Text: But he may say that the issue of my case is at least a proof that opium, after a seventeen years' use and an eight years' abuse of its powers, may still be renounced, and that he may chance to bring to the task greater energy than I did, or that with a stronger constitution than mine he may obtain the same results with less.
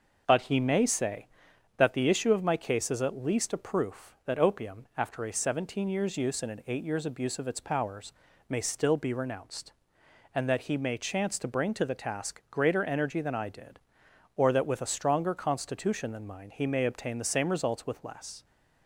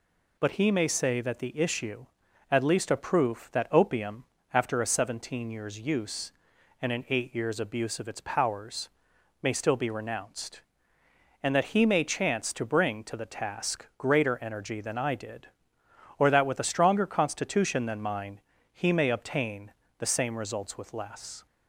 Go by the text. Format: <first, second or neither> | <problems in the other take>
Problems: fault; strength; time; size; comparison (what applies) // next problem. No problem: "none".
first | skips "of my case is"; at 2.2 s // pauses between "mine" and "he"; slight; at 18.3 s; 0.32 s long // pauses between "obtain" and "the"; slight; at 19.7 s; 0.26 s long